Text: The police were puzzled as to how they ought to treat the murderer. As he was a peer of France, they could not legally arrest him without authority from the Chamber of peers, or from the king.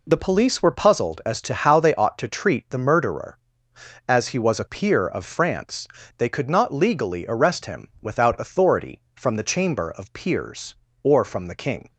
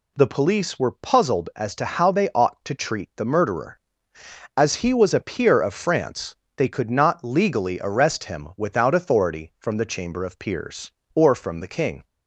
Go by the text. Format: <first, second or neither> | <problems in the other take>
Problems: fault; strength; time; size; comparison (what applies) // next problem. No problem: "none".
neither | none